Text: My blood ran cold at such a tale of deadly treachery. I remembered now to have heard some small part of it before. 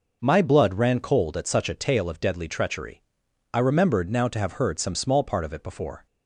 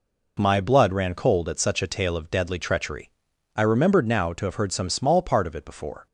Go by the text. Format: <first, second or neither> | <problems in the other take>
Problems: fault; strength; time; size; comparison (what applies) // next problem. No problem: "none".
neither | none